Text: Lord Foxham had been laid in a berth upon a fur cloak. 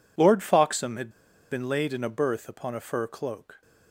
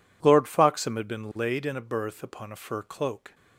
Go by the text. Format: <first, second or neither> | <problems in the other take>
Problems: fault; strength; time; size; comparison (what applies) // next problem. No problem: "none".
second | pauses between "had" and "been"; at 1.0 s; 0.41 s long